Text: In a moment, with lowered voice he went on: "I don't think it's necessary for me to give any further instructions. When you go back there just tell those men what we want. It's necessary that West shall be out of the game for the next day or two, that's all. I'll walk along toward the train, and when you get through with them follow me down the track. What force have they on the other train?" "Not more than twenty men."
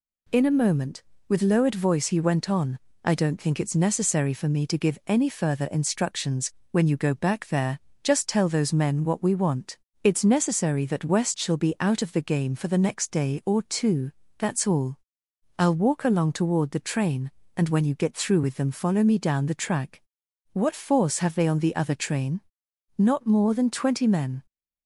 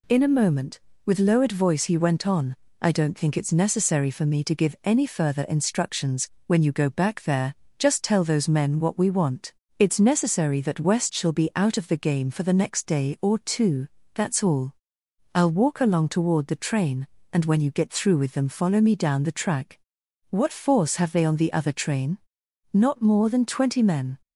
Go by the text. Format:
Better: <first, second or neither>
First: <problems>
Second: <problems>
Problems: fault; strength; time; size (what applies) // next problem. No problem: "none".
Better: neither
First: pauses between "there" and "just"; slight; at 7.7 s; 0.24 s long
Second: pauses between "there" and "just"; slight; at 7.5 s; 0.24 s long